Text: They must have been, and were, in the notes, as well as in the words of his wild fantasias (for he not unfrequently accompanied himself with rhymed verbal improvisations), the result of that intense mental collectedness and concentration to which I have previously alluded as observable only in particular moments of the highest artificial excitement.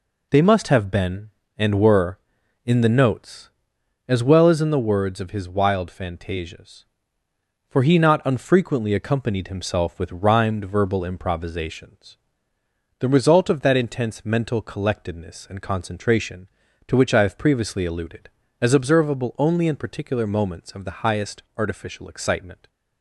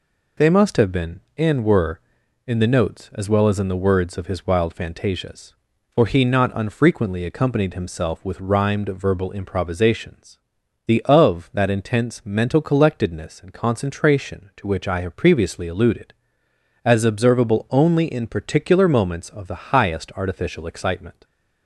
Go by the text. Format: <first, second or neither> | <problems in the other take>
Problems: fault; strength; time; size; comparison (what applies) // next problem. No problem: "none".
first | skips "result"; at 11.0 s